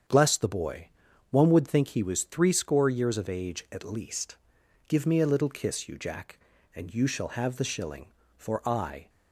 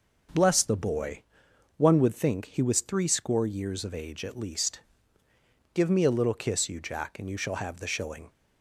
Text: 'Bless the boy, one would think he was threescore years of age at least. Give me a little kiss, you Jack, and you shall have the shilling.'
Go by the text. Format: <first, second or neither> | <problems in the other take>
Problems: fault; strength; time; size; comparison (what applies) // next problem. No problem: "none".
second | starts louder than the rest; strong; until 1.5 s; 7.5 dB // goes on to say "For I"; noticeable; from 8.3 s on; 0.72 s long